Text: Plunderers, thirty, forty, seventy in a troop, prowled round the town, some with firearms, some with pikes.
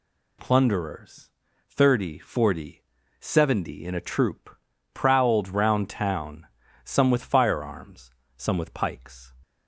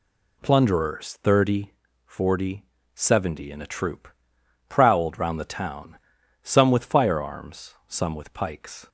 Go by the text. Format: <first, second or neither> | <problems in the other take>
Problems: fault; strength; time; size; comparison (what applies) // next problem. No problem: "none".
second | skips "the"; at 5.8 s